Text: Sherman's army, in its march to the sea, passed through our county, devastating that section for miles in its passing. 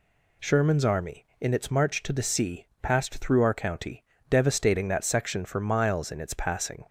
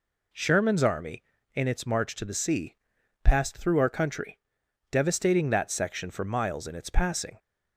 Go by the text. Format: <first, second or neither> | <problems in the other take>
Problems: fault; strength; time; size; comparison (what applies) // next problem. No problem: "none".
first | says "country" for "county"; at 3.8 s